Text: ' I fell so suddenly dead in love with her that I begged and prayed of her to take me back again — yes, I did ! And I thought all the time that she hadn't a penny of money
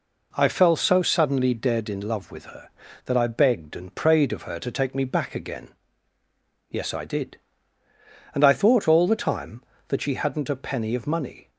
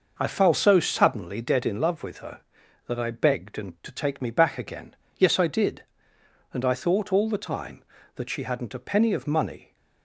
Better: first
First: none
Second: skips "prayed of her"; at 3.7 s

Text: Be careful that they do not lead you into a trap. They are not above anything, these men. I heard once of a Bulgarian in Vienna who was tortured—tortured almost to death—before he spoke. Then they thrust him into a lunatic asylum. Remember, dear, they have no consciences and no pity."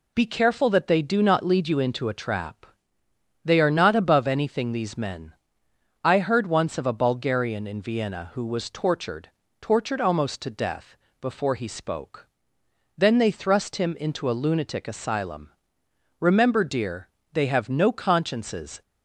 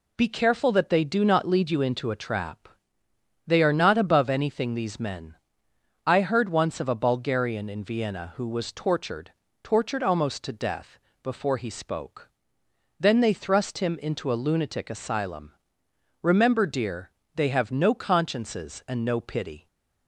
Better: second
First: stops before "and no pity"; at 18.8 s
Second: none

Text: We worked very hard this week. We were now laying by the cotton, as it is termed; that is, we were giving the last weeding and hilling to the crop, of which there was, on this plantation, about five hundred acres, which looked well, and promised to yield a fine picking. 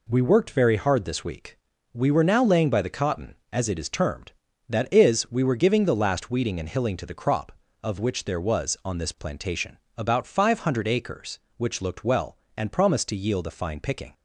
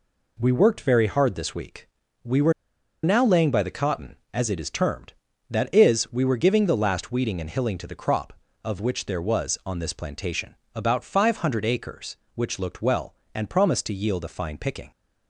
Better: first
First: none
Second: pauses between "were" and "now"; noticeable; at 2.5 s; 0.51 s long

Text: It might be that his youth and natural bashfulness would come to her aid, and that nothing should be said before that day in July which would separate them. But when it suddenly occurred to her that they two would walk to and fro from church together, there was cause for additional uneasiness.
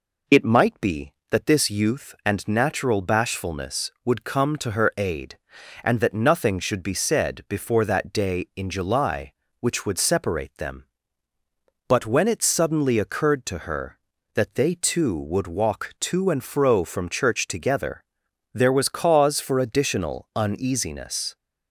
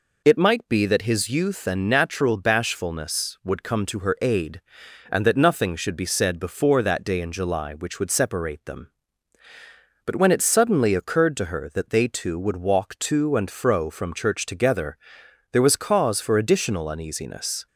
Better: second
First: says "this" for "his"; at 1.4 s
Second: none

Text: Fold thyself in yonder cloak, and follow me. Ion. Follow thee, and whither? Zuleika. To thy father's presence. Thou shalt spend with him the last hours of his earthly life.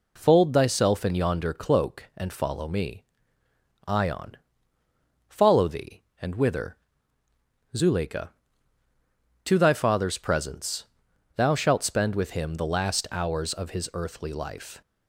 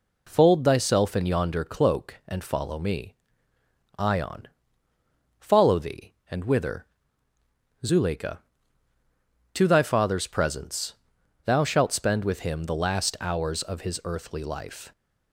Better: neither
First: none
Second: none

